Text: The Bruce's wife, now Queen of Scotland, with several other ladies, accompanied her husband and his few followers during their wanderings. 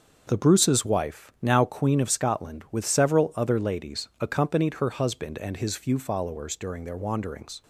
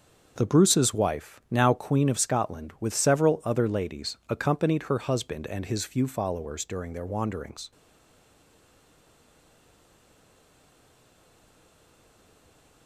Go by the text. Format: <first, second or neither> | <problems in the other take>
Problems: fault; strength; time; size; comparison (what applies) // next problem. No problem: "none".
first | starts louder than the rest; until 1.3 s; 6.5 dB; also in the first // stays silent after the last word; strong; from 7.7 s on; 5.1 s long